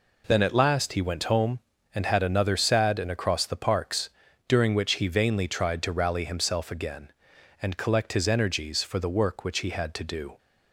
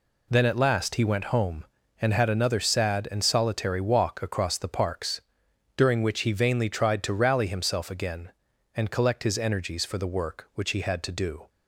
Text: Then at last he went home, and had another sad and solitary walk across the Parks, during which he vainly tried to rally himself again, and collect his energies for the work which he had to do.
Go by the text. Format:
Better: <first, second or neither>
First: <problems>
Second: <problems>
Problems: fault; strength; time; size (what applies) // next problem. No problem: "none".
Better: second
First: skips "solitary walk"; at 3.1 s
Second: none